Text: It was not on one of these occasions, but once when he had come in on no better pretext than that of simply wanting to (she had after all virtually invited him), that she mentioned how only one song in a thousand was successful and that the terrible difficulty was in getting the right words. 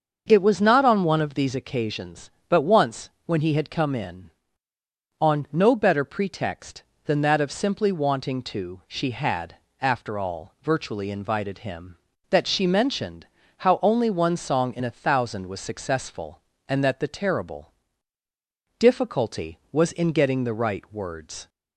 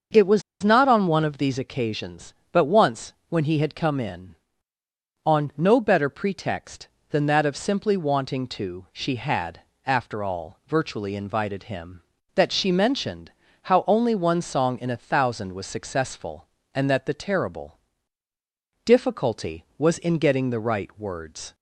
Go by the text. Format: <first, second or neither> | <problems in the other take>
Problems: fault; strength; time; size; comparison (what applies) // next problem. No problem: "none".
first | starts louder than the rest; until 1.3 s; 6.5 dB; also in the first // pauses between "was" and "not"; slight; at 0.4 s; 0.20 s long // pauses between "once" and "when"; slight; at 3.1 s; 0.16 s long; slight in the first // pauses between "had" and "after"; slight; at 9.5 s; 0.26 s long; slight in the first // pauses between "mentioned" and "how"; slight; at 13.3 s; 0.30 s long; slight in the first // pauses between "terrible" and "difficulty"; at 17.7 s; 1.0 s long; also in the first